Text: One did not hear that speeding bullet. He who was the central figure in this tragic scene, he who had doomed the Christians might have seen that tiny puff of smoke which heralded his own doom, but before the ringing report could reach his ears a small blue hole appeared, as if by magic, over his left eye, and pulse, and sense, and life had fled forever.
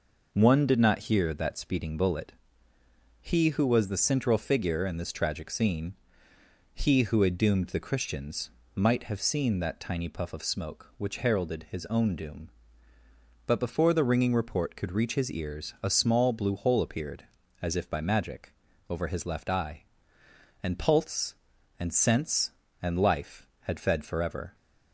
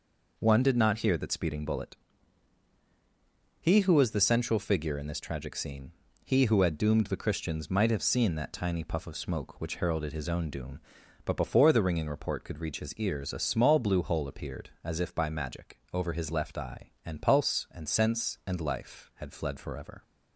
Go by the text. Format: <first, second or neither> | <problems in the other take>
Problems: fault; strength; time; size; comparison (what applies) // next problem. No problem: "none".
second | pauses between "Christians" and "might"; slight; at 8.4 s; 0.24 s long // says "fed" for "fled"; at 23.8 s